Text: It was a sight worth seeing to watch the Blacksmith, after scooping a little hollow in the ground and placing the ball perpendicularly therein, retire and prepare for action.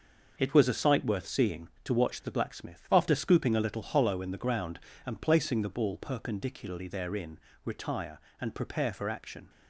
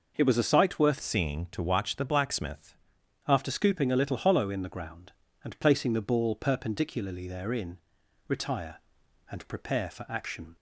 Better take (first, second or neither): first